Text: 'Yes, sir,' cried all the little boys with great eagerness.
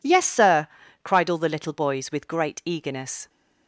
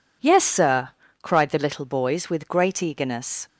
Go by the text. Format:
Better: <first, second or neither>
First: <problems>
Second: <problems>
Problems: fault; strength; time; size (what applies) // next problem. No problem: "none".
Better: first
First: none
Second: skips "all"; at 1.5 s